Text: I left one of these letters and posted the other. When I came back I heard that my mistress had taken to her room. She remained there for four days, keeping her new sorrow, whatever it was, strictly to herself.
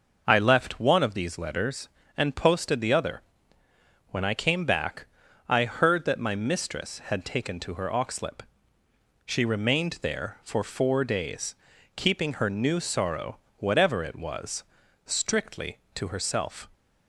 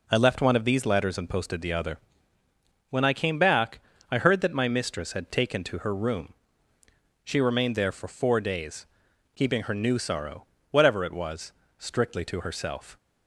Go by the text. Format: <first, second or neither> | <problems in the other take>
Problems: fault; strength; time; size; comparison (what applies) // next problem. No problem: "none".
second | pauses between "back" and "I"; at 5.0 s; 0.42 s long; slight in the second // says "oxlip" for "room"; at 7.8 s